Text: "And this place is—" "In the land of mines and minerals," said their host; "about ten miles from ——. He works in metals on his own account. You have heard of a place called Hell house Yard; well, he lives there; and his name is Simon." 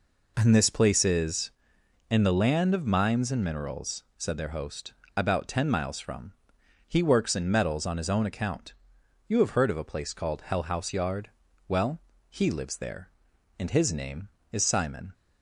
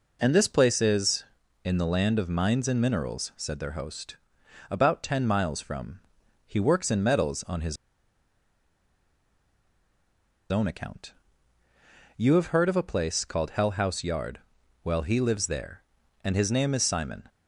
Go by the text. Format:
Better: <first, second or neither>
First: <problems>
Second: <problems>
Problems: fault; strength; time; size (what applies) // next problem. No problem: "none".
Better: first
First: none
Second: pauses between "his" and "own"; strong; at 7.7 s; 2.7 s long